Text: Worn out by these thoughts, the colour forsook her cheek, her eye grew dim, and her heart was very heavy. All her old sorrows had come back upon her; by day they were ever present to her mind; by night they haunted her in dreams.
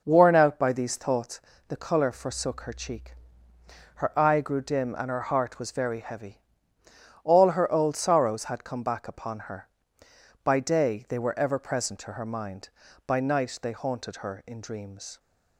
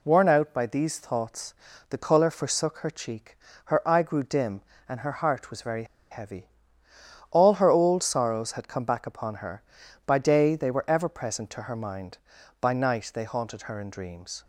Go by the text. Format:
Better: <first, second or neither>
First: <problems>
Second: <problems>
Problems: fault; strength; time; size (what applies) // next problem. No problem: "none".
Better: first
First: none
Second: pauses between "very" and "heavy"; slight; at 5.8 s; 0.27 s long